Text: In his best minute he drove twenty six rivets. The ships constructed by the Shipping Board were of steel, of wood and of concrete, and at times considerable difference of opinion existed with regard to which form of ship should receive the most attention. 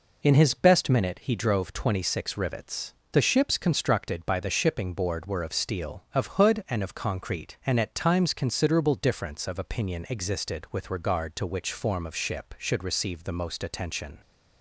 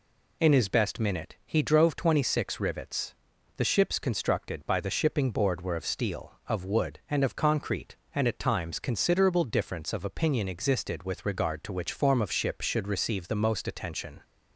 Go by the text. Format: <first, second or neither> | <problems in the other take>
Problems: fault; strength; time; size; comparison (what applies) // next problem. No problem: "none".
second | says "hood" for "wood"; at 6.3 s